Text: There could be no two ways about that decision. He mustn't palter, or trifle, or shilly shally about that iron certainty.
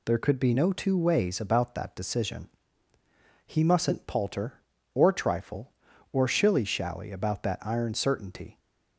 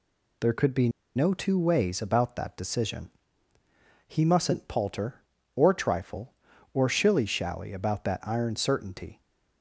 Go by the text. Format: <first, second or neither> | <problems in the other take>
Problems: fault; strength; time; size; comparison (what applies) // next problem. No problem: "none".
first | pauses between "be" and "no"; slight; at 0.8 s; 0.27 s long